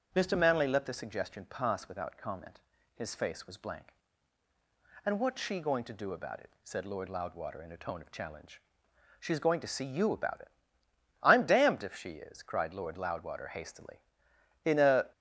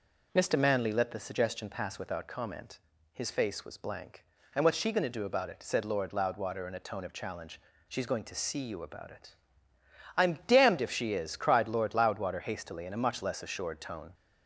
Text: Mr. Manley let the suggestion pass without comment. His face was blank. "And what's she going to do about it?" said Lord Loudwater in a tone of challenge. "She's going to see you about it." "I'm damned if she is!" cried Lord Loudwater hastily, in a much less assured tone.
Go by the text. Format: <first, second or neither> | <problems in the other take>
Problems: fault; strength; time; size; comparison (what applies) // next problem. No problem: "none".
second | starts louder than the rest; strong; until 1.1 s; 7 dB // stops before "much less assured tone"; at 15.1 s